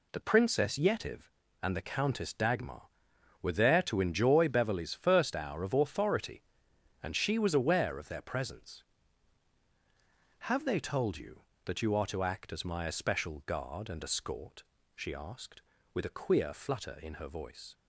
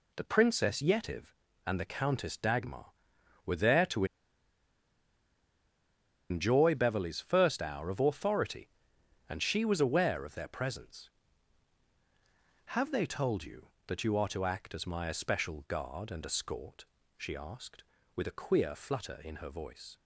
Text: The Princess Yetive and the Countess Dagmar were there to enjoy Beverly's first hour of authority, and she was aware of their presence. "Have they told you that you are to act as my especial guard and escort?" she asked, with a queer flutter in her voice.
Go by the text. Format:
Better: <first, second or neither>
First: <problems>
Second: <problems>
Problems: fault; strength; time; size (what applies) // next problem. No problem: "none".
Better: first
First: none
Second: pauses between "to" and "enjoy"; strong; at 4.0 s; 2.2 s long